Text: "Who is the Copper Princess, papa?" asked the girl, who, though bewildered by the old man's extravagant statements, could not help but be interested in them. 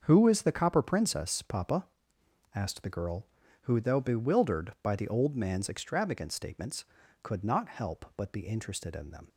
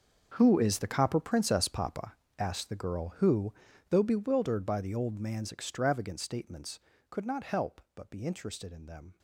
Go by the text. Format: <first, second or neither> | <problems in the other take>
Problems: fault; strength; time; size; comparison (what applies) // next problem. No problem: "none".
first | gets quieter; strong; throughout; 16 dB // starts louder than the rest; until 1.3 s; 7 dB; also in the first